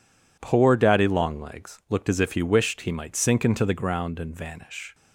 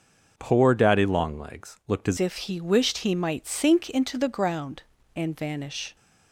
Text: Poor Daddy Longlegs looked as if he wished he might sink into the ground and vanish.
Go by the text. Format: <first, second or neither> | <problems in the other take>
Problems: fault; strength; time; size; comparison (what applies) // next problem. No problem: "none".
first | starts louder than the rest; noticeable; until 1.3 s; 6 dB // changes voice at "if"; from 2.1 s on; 3.8 s long